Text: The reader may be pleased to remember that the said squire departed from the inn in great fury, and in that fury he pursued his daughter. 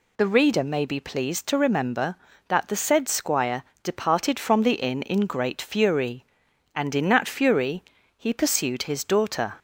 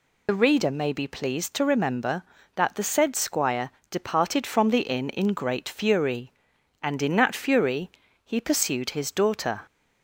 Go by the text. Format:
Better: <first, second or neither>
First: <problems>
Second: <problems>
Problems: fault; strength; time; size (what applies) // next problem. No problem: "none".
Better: first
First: pauses between "squire" and "departed"; slight; at 3.6 s; 0.20 s long // pauses between "fury" and "he"; slight; at 7.8 s; 0.34 s long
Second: loses the start of "The"; at 0.2 s; 45 ms // pauses between "squire" and "departed"; slight; at 3.7 s; 0.20 s long // pauses between "fury" and "he"; slight; at 7.9 s; 0.34 s long